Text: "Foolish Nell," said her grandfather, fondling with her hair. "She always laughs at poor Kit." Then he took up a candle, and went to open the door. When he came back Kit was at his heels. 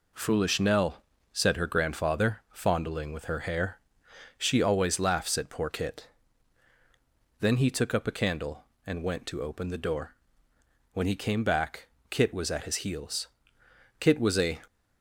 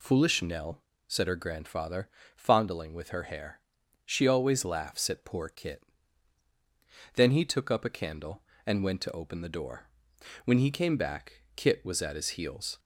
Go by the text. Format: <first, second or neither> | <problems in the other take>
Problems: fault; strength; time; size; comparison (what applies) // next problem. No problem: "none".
second | pauses between "back" and "Kit"; slight; at 11.8 s; 0.22 s long // goes on to say "Kit was a"; from 14.0 s on; 0.60 s long